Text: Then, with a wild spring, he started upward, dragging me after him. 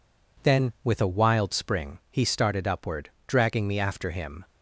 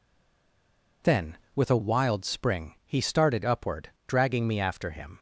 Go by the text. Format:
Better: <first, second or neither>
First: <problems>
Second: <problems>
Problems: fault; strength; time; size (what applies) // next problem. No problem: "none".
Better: first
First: none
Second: stays silent before the first word; until 1.0 s; 1.0 s long